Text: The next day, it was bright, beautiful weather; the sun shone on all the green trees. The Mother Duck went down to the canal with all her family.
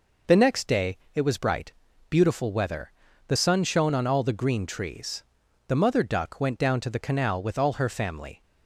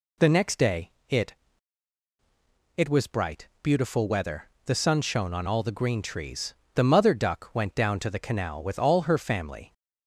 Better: first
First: none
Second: says "it" twice; at 2.7 s

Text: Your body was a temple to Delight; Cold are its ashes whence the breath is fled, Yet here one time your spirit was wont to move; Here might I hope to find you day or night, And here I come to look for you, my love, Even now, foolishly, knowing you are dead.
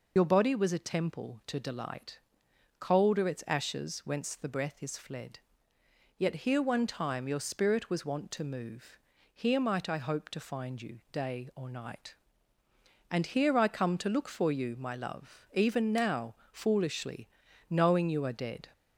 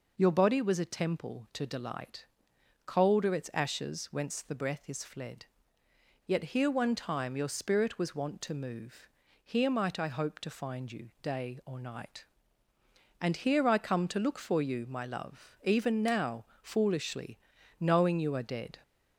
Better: second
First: loses the start of "Your"; at 0.1 s; 45 ms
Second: none

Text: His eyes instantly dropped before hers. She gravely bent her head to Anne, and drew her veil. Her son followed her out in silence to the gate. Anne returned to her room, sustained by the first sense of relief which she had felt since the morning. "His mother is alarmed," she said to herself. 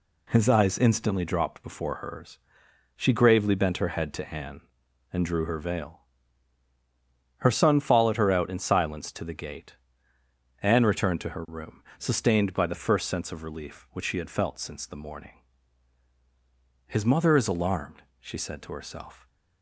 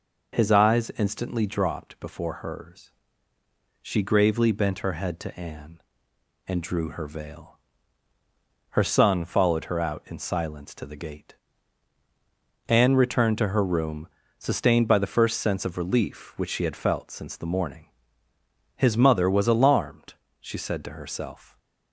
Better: first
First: none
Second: says "was" for "is"; at 19.2 s

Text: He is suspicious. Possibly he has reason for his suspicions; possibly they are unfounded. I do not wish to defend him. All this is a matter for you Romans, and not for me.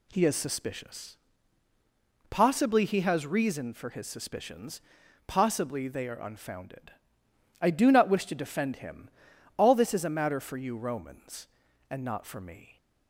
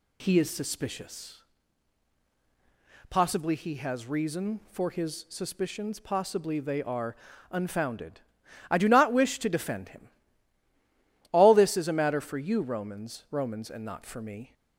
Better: first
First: none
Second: pauses between "are" and "unfounded"; slight; at 7.1 s; 0.36 s long // says "Romans" twice; at 13.3 s

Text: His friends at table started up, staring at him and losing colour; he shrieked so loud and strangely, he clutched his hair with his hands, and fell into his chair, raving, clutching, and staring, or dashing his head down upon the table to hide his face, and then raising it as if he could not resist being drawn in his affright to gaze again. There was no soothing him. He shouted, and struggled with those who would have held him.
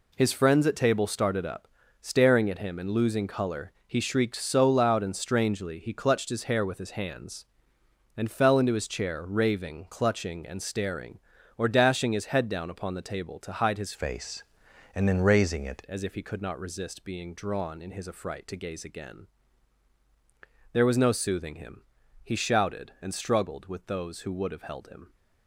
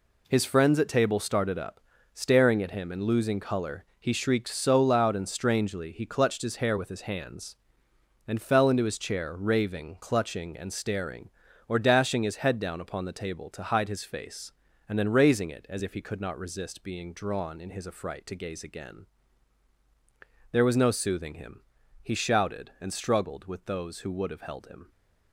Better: second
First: changes voice from "face" to "it"; from 13.9 to 15.8 s; 1.9 s long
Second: none

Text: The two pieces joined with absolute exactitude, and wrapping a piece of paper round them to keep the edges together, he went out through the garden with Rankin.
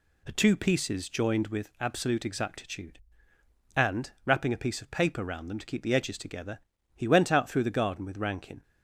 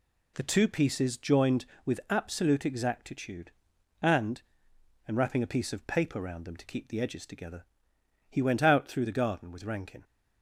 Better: first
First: none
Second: says "and" twice; at 5.0 s

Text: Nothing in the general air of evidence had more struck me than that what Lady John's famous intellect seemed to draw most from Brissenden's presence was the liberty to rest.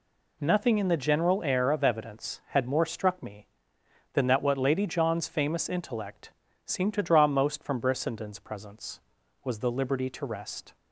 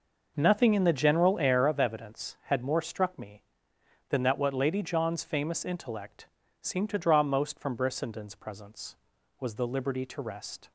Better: first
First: pauses between "intellect" and "seemed"; slight; at 6.3 s; 0.34 s long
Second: starts louder than the rest; noticeable; until 1.8 s; 5.5 dB // pauses between "intellect" and "seemed"; slight; at 6.2 s; 0.34 s long

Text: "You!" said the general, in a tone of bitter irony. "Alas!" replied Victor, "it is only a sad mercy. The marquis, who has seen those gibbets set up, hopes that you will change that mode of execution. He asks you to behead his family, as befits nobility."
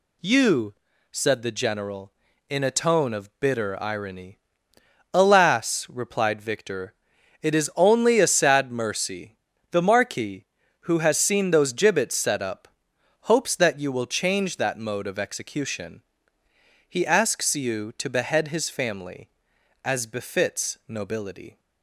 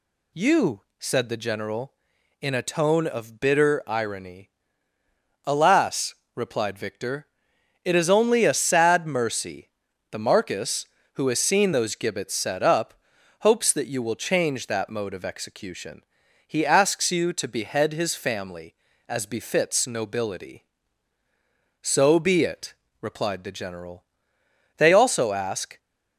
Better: first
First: none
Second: goes on to say "So be it replied the general They also ask"; strong; from 21.8 s on; 3.9 s long

